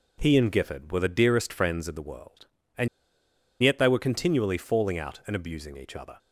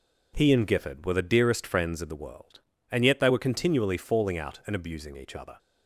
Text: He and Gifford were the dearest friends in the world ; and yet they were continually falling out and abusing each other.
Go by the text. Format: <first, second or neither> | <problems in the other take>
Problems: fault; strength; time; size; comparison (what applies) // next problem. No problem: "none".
second | pauses between "and" and "yet"; noticeable; at 2.8 s; 0.75 s long